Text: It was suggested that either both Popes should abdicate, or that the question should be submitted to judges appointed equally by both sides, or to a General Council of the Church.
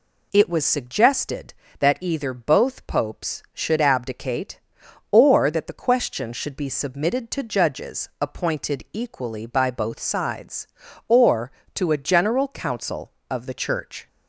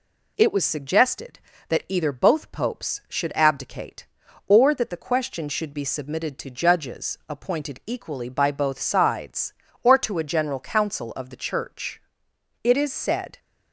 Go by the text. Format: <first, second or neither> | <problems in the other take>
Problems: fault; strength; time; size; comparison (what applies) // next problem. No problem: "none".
first | goes on to say "It is said"; noticeable; from 12.6 s on; 0.76 s long